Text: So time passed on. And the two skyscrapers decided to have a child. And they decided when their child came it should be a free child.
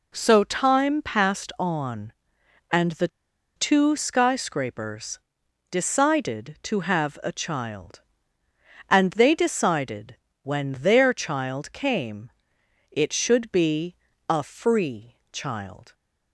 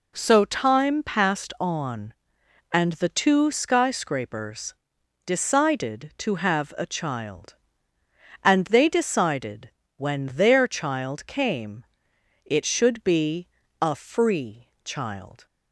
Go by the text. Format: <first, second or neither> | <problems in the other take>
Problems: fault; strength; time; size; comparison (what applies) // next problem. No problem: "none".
second | pauses between "the" and "two"; noticeable; at 3.0 s; 0.48 s long // pauses between "skyscrapers" and "decided"; noticeable; at 5.1 s; 0.52 s long; noticeable in the second // pauses between "decided" and "when"; slight; at 10.1 s; 0.26 s long; slight in the second // pauses between "came" and "it"; noticeable; at 12.2 s; 0.62 s long; noticeable in the second // pauses between "be" and "a"; slight; at 13.9 s; 0.32 s long; slight in the second // pauses between "free" and "child"; slight; at 15.1 s; 0.16 s long; slight in the second